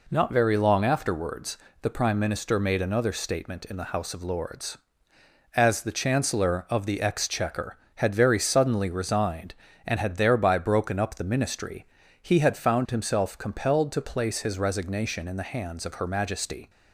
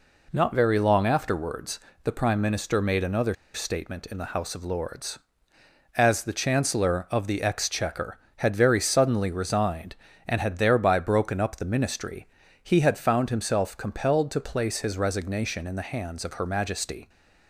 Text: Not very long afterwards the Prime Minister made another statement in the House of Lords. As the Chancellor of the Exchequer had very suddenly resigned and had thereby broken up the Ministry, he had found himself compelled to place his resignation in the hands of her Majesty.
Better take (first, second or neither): first